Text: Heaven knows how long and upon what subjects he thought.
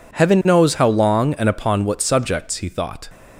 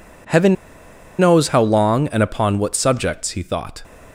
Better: first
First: none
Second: pauses between "Heaven" and "knows"; noticeable; at 0.5 s; 0.63 s long

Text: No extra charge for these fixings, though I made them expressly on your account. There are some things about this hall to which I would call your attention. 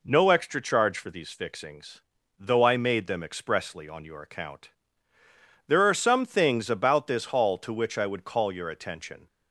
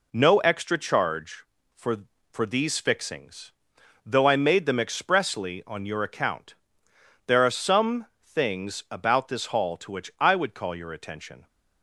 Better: first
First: none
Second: says "for" twice; at 2.3 s // pauses between "some" and "things"; slight; at 8.0 s; 0.20 s long

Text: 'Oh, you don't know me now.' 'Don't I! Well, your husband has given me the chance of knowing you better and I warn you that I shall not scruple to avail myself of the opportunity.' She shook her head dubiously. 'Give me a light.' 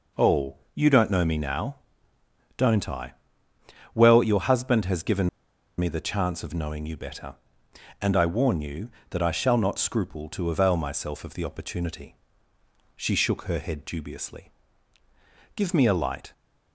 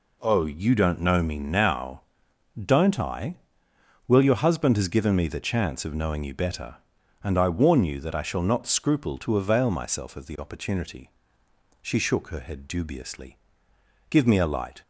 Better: second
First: pauses between "given" and "me"; noticeable; at 5.2 s; 0.49 s long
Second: none

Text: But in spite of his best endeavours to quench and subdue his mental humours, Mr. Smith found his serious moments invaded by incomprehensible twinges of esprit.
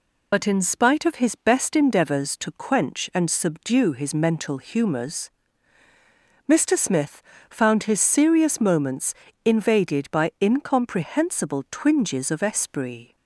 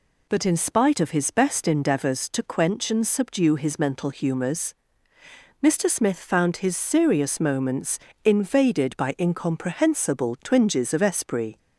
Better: second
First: loses the start of "But"; at 0.3 s; 65 ms // pauses between "Smith" and "found"; slight; at 7.2 s; 0.28 s long // pauses between "moments" and "invaded"; slight; at 9.1 s; 0.30 s long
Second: pauses between "moments" and "invaded"; slight; at 7.9 s; 0.26 s long

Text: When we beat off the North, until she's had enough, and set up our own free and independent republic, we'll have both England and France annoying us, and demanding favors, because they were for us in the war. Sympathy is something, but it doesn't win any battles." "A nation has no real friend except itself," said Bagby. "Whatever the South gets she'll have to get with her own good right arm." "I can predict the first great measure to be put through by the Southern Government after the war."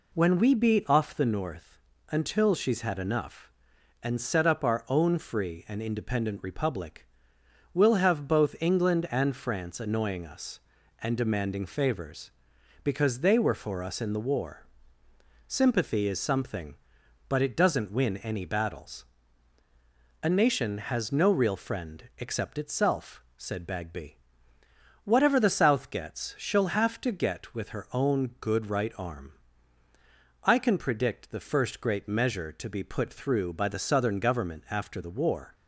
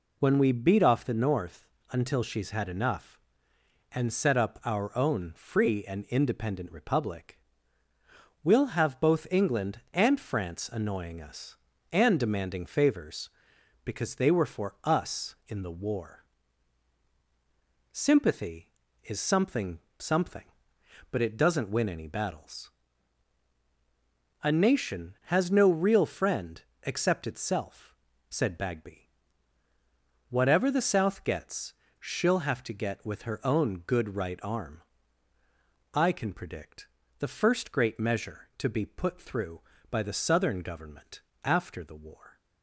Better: first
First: none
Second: says "something" twice; at 19.9 s // pauses between "friend" and "except"; slight; at 26.6 s; 0.22 s long // pauses between "gets" and "she'll"; slight; at 31.7 s; 0.26 s long // pauses between "predict" and "the"; slight; at 36.8 s; 0.32 s long // pauses between "Government" and "after"; slight; at 41.2 s; 0.22 s long

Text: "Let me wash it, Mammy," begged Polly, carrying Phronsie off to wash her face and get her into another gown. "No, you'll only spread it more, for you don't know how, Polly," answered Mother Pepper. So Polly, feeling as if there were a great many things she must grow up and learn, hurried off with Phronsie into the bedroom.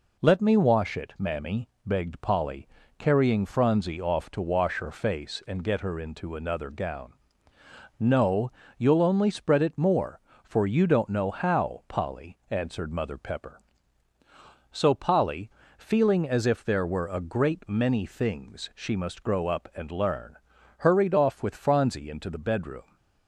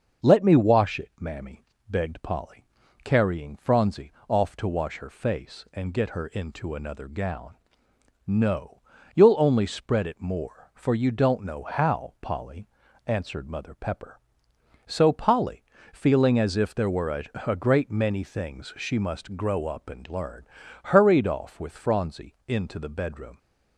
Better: first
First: none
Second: starts louder than the rest; until 1.3 s; 6.5 dB // pauses between "Phronsie" and "off"; slight; at 4.1 s; 0.16 s long // says "a" twice; at 17.4 s

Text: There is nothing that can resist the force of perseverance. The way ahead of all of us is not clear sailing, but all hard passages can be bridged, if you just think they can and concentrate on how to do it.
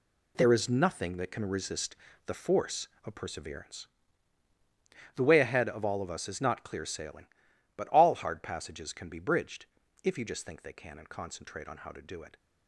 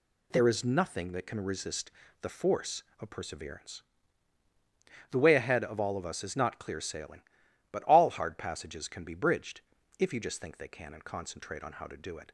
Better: second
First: gets quieter; strong; throughout; 10 dB // pauses between "resist" and "the"; slight; at 1.9 s; 0.30 s long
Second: pauses between "resist" and "the"; slight; at 1.9 s; 0.30 s long

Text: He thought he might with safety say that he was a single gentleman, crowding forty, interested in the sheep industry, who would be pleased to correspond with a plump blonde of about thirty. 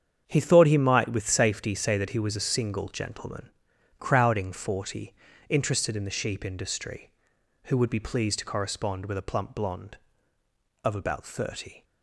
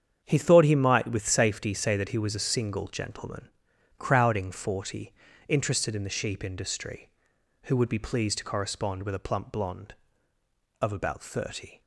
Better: neither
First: starts louder than the rest; strong; until 1.2 s; 8 dB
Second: starts louder than the rest; strong; until 1.2 s; 8 dB

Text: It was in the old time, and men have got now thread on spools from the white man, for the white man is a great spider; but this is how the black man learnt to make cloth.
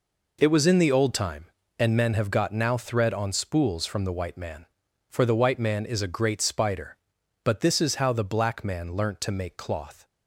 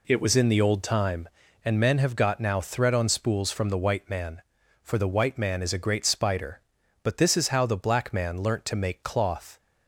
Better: neither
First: none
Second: none

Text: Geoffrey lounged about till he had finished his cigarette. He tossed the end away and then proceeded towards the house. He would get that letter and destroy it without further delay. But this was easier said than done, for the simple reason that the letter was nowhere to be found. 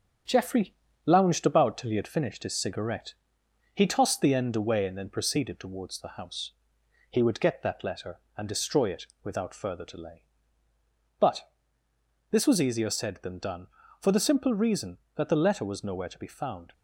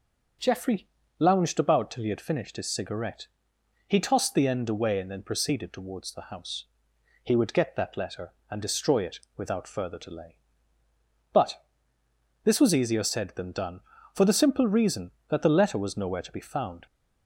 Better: second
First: gets quieter; noticeable; throughout; 4 dB // pauses between "Geoffrey" and "lounged"; slight; at 0.7 s; 0.30 s long // pauses between "it" and "without"; slight; at 9.0 s; 0.16 s long // pauses between "But" and "this"; noticeable; at 11.4 s; 0.82 s long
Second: pauses between "Geoffrey" and "lounged"; slight; at 0.8 s; 0.30 s long // pauses between "it" and "without"; slight; at 9.1 s; 0.16 s long // pauses between "But" and "this"; noticeable; at 11.6 s; 0.82 s long

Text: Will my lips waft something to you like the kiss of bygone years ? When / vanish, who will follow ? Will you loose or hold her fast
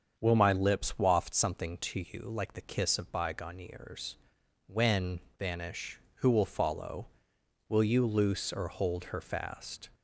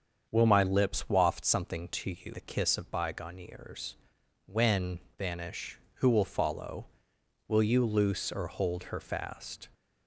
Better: first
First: starts louder than the rest; until 1.1 s; 7 dB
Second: starts louder than the rest; strong; until 1.3 s; 7 dB // skips "like"; at 2.3 s

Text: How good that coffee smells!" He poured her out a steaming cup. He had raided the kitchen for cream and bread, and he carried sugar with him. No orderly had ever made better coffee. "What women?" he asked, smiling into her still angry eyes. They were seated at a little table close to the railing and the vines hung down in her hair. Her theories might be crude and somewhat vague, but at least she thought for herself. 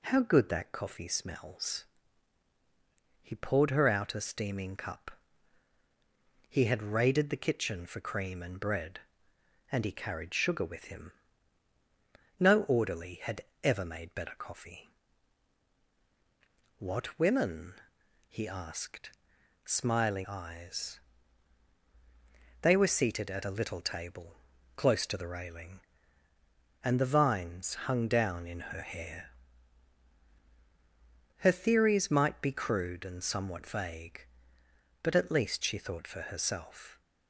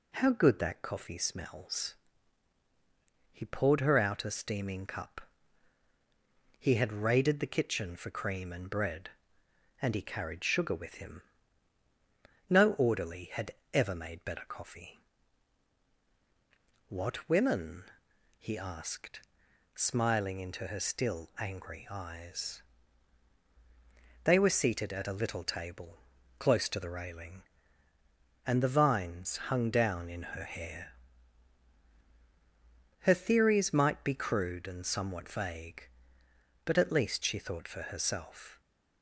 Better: second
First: pauses between "had" and "ever"; slight; at 13.4 s; 0.22 s long // skips "into her still angry"; at 20.2 s // pauses between "table" and "close"; at 24.3 s; 0.40 s long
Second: pauses between "had" and "ever"; slight; at 13.5 s; 0.22 s long // pauses between "table" and "close"; at 25.9 s; 0.40 s long

